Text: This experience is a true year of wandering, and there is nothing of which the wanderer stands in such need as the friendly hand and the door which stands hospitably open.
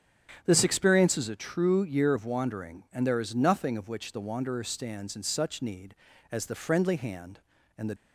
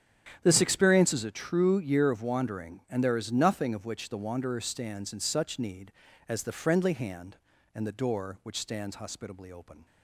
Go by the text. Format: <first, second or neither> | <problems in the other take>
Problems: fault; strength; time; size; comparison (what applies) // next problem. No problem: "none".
second | starts louder than the rest; strong; until 1.4 s; 9 dB; strong in the second // stops before "door which stands hospitably open"; at 7.9 s